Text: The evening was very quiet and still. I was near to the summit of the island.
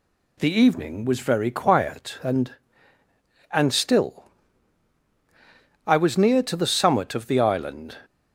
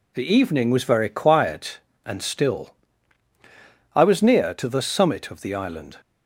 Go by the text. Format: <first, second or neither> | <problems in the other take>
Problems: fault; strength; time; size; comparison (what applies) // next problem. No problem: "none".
second | says "and" twice; at 3.5 s